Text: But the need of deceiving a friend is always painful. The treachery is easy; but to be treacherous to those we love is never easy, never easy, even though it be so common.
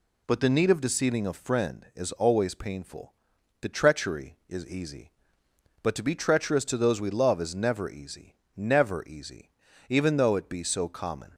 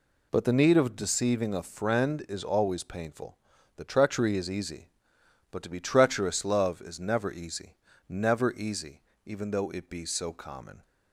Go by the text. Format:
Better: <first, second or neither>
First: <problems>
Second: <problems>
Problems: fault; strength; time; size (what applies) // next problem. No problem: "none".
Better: first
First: none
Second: skips "to those we"; at 6.4 s